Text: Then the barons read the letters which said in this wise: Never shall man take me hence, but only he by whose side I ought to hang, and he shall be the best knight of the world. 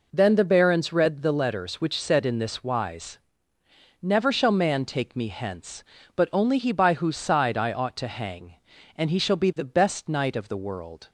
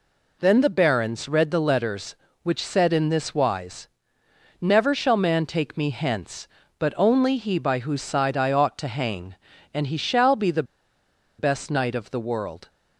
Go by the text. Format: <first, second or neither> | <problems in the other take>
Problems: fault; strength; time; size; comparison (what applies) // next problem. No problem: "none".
first | pauses between "the" and "best"; noticeable; at 10.6 s; 0.75 s long